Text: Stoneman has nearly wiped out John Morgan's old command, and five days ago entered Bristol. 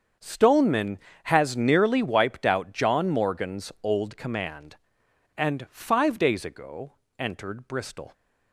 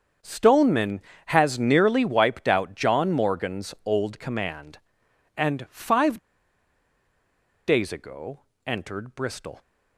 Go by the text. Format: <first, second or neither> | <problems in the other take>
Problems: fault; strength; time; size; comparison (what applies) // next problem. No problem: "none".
first | starts louder than the rest; strong; until 1.4 s; 7 dB; strong in the first // pauses between "five" and "days"; strong; at 6.1 s; 1.4 s long // pauses between "ago" and "entered"; slight; at 8.4 s; 0.26 s long; slight in the first